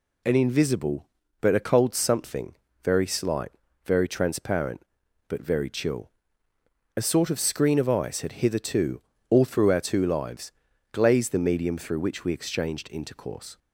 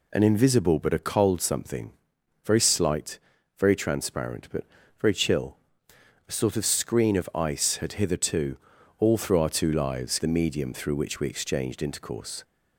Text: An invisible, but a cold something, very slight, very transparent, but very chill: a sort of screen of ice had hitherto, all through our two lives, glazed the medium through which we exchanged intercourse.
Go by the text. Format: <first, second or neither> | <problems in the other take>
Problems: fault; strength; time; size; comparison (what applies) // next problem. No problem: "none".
first | pauses between "but" and "very"; slight; at 4.6 s; 0.34 s long // skips "glazed"; at 10.1 s